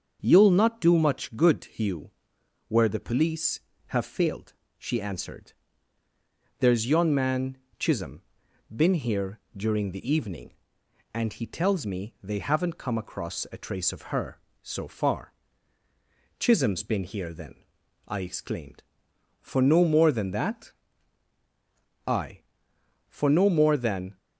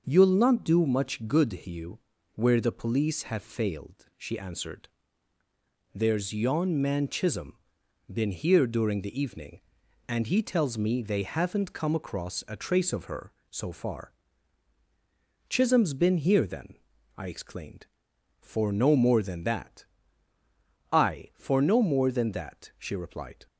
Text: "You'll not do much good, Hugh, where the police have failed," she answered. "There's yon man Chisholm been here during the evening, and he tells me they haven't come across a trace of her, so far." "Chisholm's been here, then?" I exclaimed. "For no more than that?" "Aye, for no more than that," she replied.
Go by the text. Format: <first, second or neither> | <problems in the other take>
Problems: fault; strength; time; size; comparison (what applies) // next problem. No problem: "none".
second | starts louder than the rest; until 1.2 s; 6.5 dB; noticeable in the second // pauses between "man" and "Chisholm"; slight; at 7.5 s; 0.22 s long // pauses between "Chisholm" and "been"; noticeable; at 8.1 s; 0.50 s long; noticeable in the second // pauses between "here" and "during"; slight; at 9.3 s; 0.16 s long // stops before "that she replied"; at 24.1 s